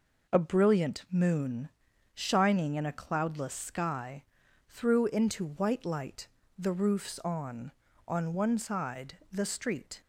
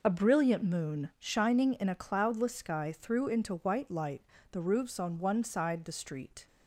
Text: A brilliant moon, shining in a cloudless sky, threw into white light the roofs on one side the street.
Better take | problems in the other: second | pauses between "light" and "the"; slight; at 6.2 s; 0.30 s long; slight in the second // says "on" twice; at 8.0 s

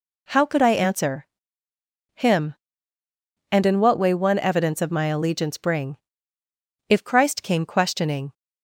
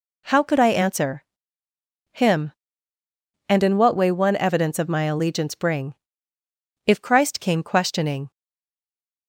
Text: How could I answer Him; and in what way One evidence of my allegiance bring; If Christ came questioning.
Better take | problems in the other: first | pauses between "answer" and "Him"; noticeable; at 1.2 s; 0.88 s long; noticeable in the first // stays silent after the last word; from 8.3 s on; 0.9 s long

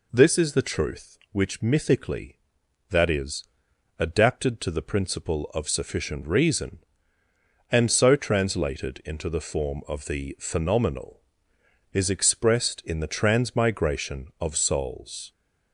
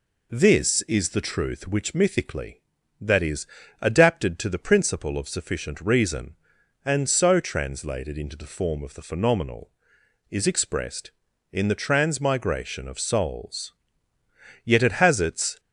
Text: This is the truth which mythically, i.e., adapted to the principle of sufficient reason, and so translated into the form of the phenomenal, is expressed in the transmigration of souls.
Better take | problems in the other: first | goes on to say "Yet it has its"; noticeable; from 14.6 s on; 0.96 s long

